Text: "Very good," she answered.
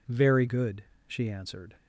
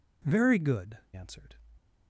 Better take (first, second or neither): first